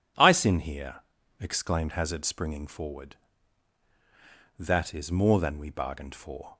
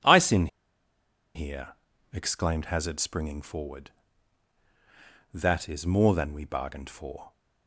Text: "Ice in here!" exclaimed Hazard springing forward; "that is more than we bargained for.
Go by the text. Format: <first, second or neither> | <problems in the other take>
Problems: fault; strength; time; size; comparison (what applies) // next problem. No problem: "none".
first | pauses between "in" and "here"; noticeable; at 0.4 s; 0.87 s long